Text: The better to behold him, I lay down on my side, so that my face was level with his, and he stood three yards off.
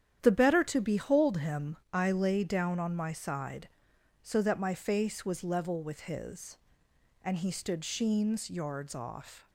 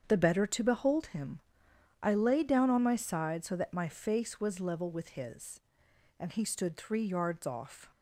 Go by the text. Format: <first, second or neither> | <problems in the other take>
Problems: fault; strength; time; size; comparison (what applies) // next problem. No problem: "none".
second | starts louder than the rest; strong; until 1.2 s; 10 dB; strong in the second // says "sheens" for "three"; at 7.8 s